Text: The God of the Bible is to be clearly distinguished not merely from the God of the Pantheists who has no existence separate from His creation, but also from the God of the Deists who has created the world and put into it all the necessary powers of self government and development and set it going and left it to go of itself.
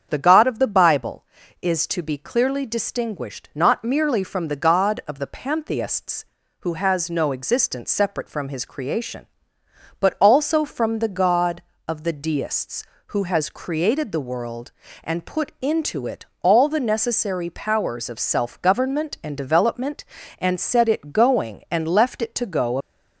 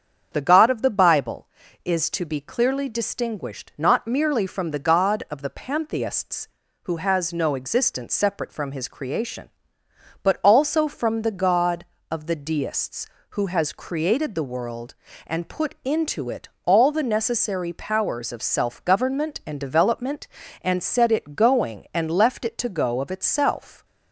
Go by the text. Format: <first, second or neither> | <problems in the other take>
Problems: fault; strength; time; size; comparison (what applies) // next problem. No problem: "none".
second | starts louder than the rest; strong; until 1.1 s; 7.5 dB; strong in the second // pauses between "it" and "all"; slight; at 16.2 s; 0.16 s long; slight in the second // stops before "of itself"; at 22.8 s